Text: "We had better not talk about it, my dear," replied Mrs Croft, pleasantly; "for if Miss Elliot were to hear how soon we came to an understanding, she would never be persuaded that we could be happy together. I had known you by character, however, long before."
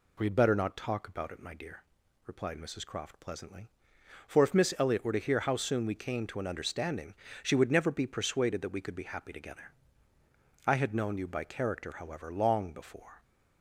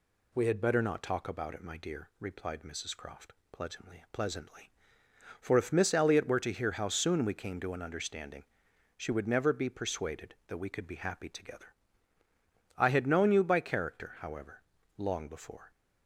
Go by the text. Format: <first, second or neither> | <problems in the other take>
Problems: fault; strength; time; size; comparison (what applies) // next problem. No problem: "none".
first | says "pleasantly" twice; at 4.1 s